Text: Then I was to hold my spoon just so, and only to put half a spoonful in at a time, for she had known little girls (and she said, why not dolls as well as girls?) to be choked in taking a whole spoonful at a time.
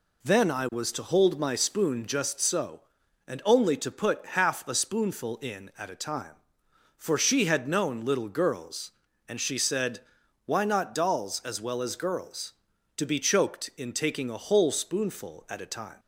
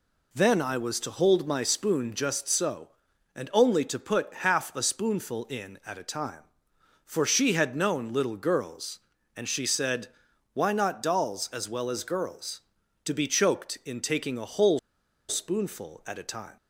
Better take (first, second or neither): first